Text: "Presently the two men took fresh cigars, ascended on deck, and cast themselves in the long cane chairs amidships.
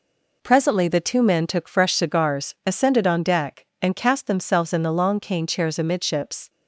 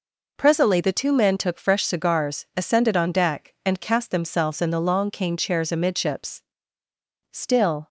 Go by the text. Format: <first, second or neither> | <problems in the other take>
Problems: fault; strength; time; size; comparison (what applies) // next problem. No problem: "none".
first | goes on to say "Still"; from 7.3 s on; 0.56 s long